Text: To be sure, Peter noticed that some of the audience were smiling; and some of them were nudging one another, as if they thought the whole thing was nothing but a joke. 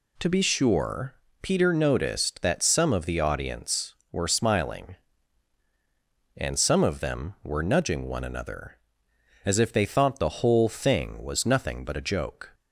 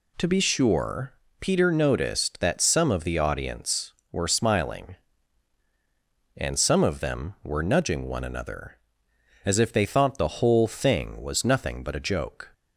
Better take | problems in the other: neither | none

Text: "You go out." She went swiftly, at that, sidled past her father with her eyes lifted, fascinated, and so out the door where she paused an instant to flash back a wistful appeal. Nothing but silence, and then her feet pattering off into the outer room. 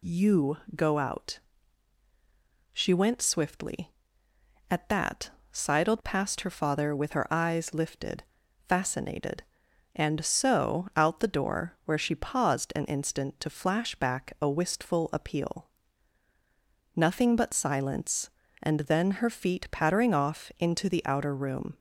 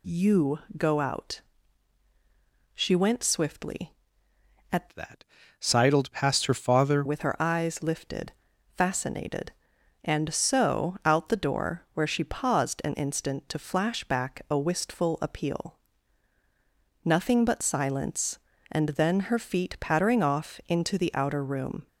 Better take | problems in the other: first | pauses between "You" and "go"; slight; at 0.5 s; 0.18 s long; slight in the first // changes voice from "that" to "father"; from 4.9 to 7.0 s; 2.1 s long

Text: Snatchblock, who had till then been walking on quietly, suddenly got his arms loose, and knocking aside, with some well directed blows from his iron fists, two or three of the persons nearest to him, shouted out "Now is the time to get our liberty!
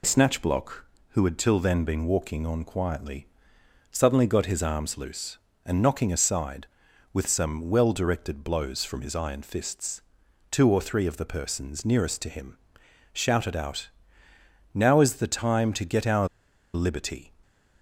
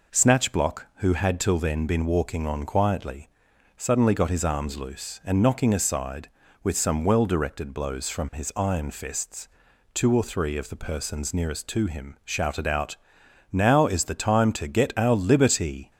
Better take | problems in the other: second | pauses between "out" and "Now"; noticeable; at 13.8 s; 0.84 s long; noticeable in the second // pauses between "our" and "liberty"; noticeable; at 16.2 s; 0.46 s long

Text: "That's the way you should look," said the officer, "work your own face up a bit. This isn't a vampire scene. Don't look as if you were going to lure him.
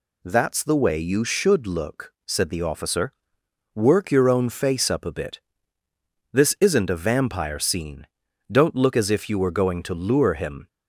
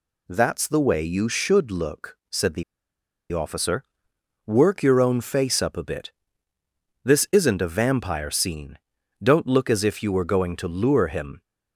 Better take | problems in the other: first | pauses between "the" and "officer"; noticeable; at 2.6 s; 0.69 s long

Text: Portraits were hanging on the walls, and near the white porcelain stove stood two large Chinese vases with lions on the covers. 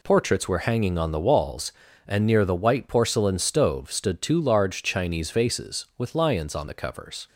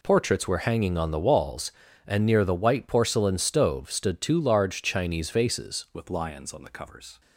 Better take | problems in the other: first | changes voice at "with"; from 5.9 s on; 1.2 s long

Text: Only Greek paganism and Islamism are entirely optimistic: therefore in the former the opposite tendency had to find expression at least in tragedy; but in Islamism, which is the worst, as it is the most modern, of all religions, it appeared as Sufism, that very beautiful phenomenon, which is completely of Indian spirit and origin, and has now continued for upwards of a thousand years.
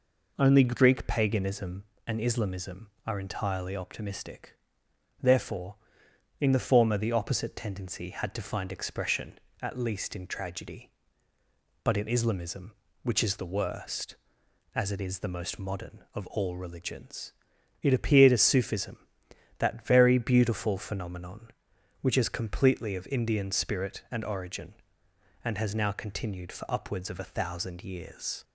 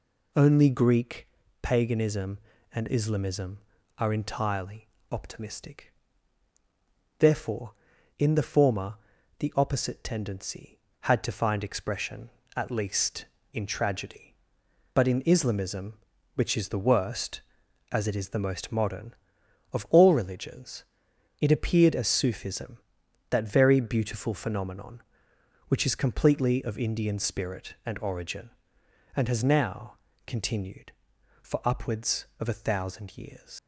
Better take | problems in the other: first | pauses between "Greek" and "paganism"; slight; at 1.2 s; 0.34 s long // pauses between "entirely" and "optimistic"; slight; at 4.8 s; 0.24 s long // pauses between "former" and "the"; at 8.9 s; 0.44 s long // pauses between "now" and "continued"; slight; at 29.9 s; 0.32 s long // leaves "years" unfinished; at 33.5 s; 90 ms

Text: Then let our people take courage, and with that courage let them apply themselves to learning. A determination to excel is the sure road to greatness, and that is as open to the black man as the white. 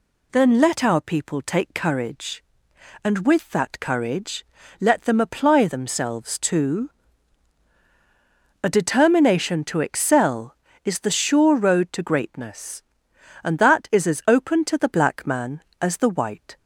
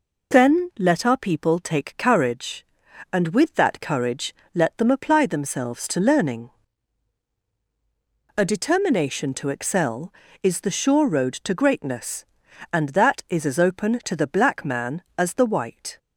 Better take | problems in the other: second | pauses between "courage" and "let"; slight; at 4.4 s; 0.34 s long; slight in the second // skips "learning"; at 7.7 s

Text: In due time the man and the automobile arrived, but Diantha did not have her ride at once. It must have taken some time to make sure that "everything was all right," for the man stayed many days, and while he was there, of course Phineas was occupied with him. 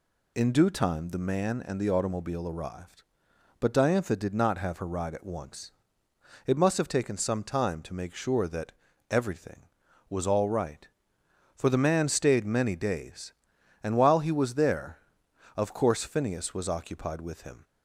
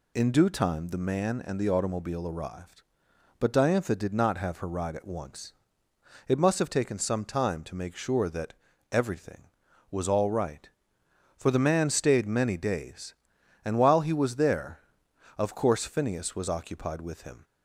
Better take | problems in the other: neither | pauses between "that" and "everything"; the same in both

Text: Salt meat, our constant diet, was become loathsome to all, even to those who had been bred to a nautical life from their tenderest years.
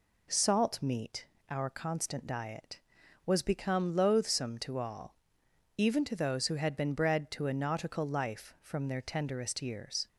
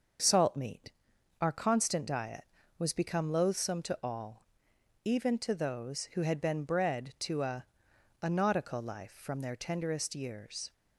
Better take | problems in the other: first | starts louder than the rest; until 1.7 s; 6.5 dB // says "a" twice; at 8.2 s

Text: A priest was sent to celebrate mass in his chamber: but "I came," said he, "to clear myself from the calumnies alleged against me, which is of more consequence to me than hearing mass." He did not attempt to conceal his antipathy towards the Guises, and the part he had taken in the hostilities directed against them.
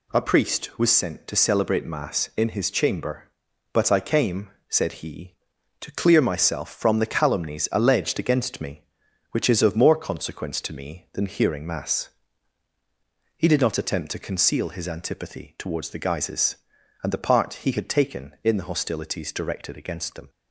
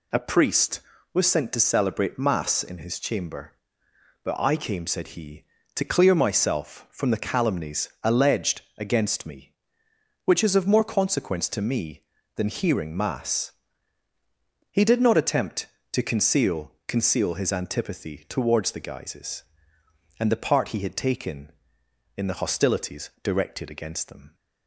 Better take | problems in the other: first | pauses between "calumnies" and "alleged"; slight; at 7.8 s; 0.16 s long // pauses between "alleged" and "against"; slight; at 8.6 s; 0.16 s long // says "conceal" twice; at 16.8 s

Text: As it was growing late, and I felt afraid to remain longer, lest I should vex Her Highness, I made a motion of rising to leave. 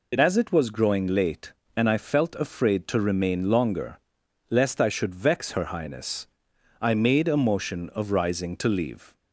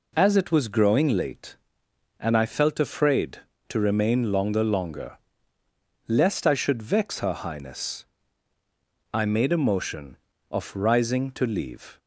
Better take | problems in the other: first | says "longer" twice; at 4.6 s

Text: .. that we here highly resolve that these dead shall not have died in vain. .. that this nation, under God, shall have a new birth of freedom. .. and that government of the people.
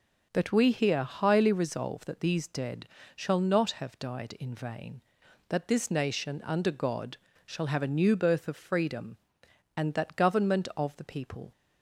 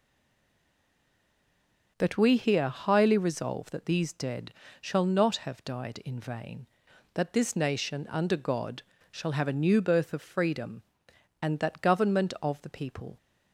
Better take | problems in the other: first | stays silent before the first word; noticeable; until 1.9 s; 1.9 s long // pauses between "dead" and "shall"; slight; at 4.5 s; 0.28 s long; slight in the first

